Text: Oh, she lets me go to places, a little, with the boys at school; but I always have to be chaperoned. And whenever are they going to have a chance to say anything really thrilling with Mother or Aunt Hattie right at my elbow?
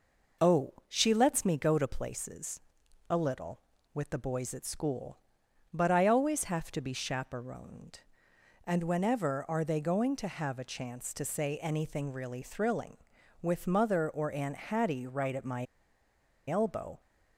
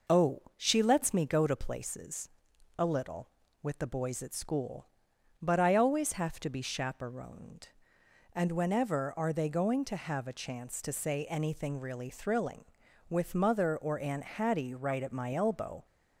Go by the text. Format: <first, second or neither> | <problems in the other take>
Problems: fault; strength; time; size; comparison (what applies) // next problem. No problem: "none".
second | pauses between "my" and "elbow"; noticeable; at 15.6 s; 0.82 s long